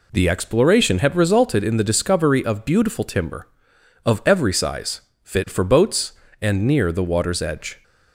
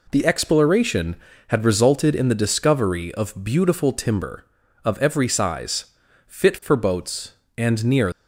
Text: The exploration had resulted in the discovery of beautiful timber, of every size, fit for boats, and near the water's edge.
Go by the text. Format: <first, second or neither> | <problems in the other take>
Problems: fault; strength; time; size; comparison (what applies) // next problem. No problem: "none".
first | stops before "the water's edge"; at 8.1 s